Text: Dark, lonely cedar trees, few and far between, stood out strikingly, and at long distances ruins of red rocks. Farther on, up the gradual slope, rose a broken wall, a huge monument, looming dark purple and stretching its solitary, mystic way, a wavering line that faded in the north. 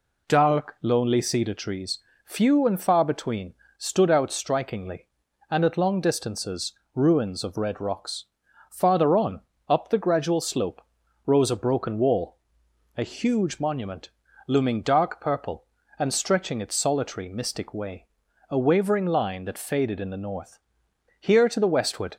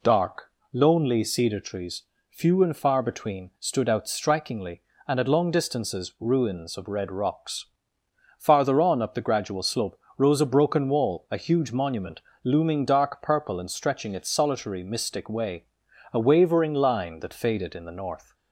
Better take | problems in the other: second | pauses between "distances" and "ruins"; slight; at 6.7 s; 0.22 s long // goes on to say "Here to the westward"; noticeable; from 21.1 s on; 0.98 s long

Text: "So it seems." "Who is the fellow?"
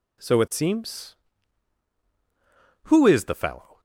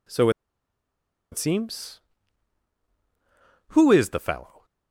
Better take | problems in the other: first | pauses between "So" and "it"; at 0.2 s; 1.0 s long

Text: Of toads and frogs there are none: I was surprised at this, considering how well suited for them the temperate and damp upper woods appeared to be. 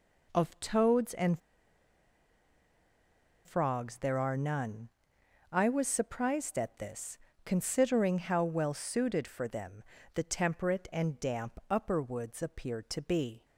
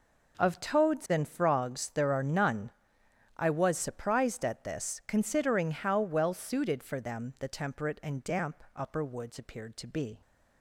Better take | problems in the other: second | pauses between "and" and "frogs"; strong; at 1.3 s; 2.0 s long // pauses between "them" and "the"; slight; at 9.8 s; 0.30 s long

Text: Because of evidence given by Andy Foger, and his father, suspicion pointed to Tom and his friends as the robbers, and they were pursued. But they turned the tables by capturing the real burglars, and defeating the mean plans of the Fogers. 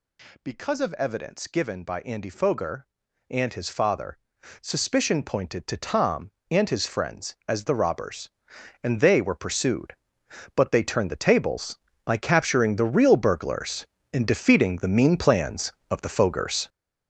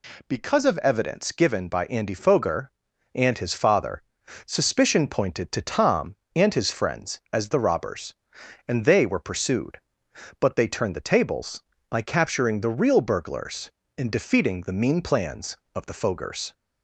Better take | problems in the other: second | gets louder; strong; throughout; 8 dB

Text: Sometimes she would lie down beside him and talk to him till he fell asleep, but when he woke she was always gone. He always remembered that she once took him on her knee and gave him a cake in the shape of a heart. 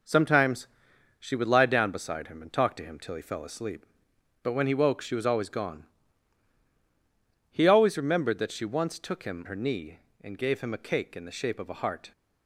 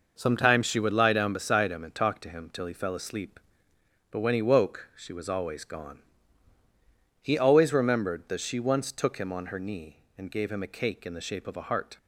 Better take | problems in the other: second | pauses between "Sometimes" and "she"; noticeable; at 0.6 s; 0.52 s long // skips "on"; at 9.4 s

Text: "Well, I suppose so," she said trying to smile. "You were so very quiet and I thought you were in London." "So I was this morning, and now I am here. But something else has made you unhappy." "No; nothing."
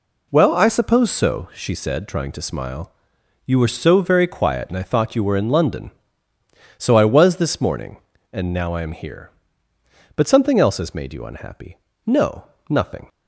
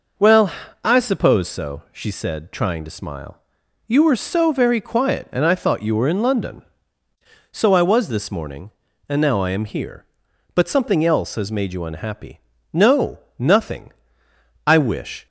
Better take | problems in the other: first | goes on to say "I wish"; from 14.6 s on; 0.60 s long

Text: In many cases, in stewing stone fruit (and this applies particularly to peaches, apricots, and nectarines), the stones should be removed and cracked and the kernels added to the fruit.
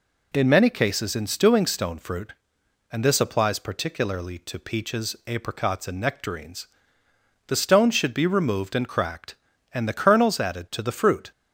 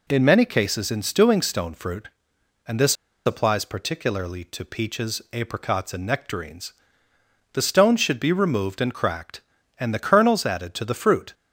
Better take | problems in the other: first | pauses between "this" and "applies"; slight; at 2.9 s; 0.30 s long

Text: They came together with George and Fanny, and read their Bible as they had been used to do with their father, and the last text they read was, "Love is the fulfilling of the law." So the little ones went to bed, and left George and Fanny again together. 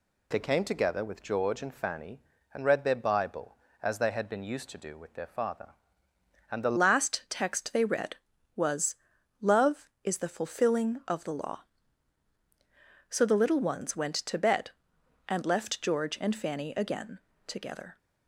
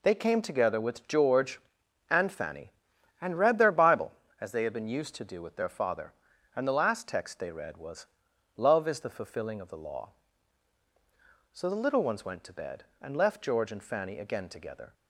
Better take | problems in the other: second | changes voice at "last"; from 6.7 s on; 11.2 s long // pauses between "again" and "together"; slight; at 17.1 s; 0.26 s long

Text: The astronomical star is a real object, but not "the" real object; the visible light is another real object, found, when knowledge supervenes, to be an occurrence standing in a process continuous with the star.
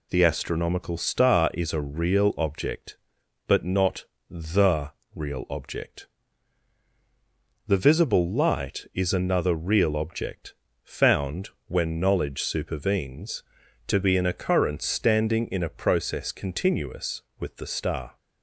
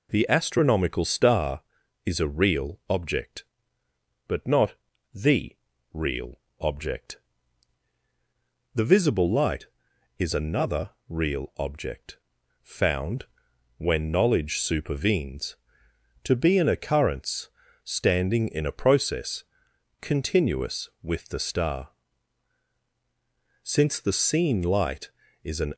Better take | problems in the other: first | pauses between "not" and "the"; at 4.7 s; 0.40 s long; slight in the first // pauses between "the" and "real"; slight; at 5.5 s; 0.36 s long; slight in the first // pauses between "real" and "object"; slight; at 6.4 s; 0.18 s long // pauses between "another" and "real"; slight; at 10.9 s; 0.18 s long // pauses between "occurrence" and "standing"; slight; at 17.4 s; 0.36 s long // pauses between "process" and "continuous"; noticeable; at 19.4 s; 0.56 s long // goes on to say "Since the seen light is an"; strong; from 23.6 s on; 2.1 s long

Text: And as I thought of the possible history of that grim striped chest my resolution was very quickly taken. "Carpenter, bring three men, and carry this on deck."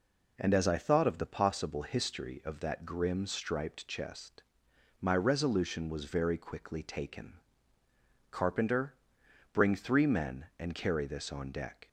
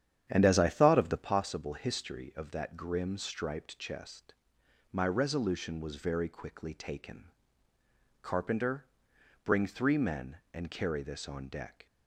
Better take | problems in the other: first | starts louder than the rest; strong; until 1.4 s; 9.5 dB // pauses between "chest" and "my"; noticeable; at 4.3 s; 0.58 s long; noticeable in the first

